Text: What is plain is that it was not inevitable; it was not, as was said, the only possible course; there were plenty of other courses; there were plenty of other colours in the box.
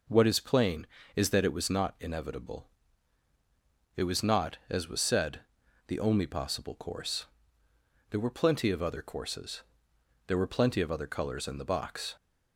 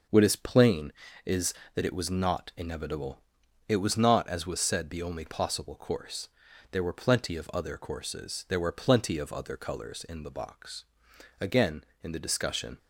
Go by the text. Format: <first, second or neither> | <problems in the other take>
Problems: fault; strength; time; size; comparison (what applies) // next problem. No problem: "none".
first | starts louder than the rest; noticeable; until 1.4 s; 6 dB // goes on to say "Again in the discussion"; from 11.3 s on; 1.3 s long